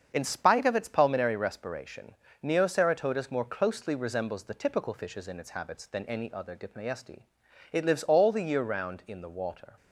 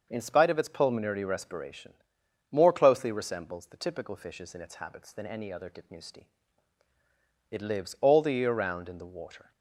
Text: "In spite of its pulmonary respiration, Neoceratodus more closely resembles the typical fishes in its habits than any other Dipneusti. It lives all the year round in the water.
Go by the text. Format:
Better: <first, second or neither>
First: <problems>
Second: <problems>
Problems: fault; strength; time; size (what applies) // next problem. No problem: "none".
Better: first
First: starts louder than the rest; until 1.1 s; 7 dB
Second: starts louder than the rest; until 1.1 s; 6 dB // skips "Neoceratodus"; at 2.2 s